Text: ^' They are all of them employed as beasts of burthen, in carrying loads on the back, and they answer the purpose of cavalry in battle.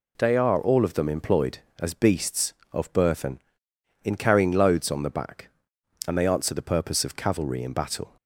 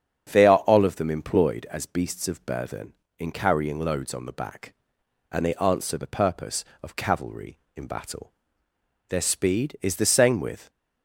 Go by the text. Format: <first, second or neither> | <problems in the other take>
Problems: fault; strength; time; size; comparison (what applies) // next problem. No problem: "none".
first | starts louder than the rest; strong; until 1.3 s; 7.5 dB // goes on to say "Their speed is the same with"; from 9.0 s on; 1.6 s long